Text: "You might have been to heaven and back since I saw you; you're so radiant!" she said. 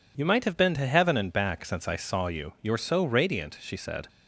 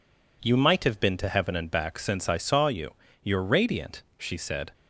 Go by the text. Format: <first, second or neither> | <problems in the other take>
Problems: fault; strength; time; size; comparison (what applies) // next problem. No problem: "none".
first | skips "so"; at 3.4 s